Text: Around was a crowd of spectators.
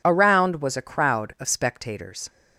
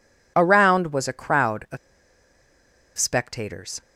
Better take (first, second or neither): first